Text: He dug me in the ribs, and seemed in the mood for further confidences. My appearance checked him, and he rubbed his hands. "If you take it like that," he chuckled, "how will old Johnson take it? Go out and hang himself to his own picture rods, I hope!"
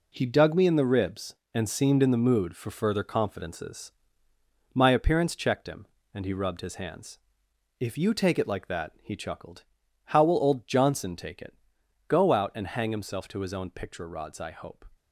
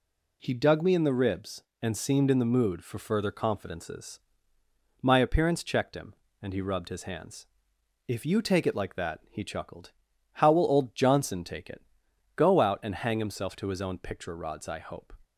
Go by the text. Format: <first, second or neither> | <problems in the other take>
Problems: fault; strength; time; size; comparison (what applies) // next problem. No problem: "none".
second | gets quieter; strong; throughout; 8 dB